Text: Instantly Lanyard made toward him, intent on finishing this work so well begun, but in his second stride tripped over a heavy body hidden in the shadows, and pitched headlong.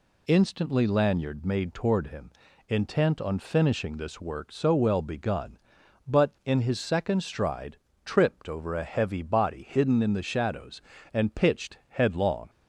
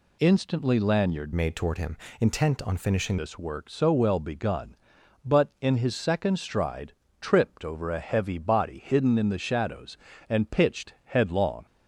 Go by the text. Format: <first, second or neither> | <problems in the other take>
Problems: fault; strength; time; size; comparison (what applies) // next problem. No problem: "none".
first | changes voice from "made" to "finishing"; from 1.3 to 3.1 s; 1.8 s long // pauses between "stride" and "tripped"; slight; at 6.9 s; 0.30 s long; slight in the first